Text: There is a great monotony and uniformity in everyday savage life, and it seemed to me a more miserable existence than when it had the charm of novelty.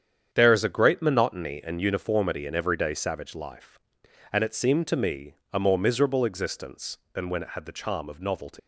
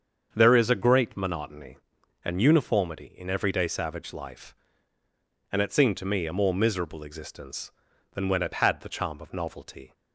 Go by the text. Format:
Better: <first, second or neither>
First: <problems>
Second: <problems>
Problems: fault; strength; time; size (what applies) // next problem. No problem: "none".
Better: second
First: starts louder than the rest; strong; until 1.3 s; 8.5 dB // pauses between "me" and "a"; slight; at 5.3 s; 0.18 s long // leaves "novelty" unfinished; at 8.5 s; 140 ms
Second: starts louder than the rest; until 1.3 s; 7 dB